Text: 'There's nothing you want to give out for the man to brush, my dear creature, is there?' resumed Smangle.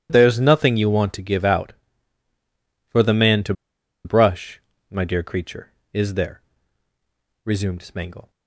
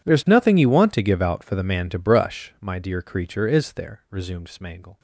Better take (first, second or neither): second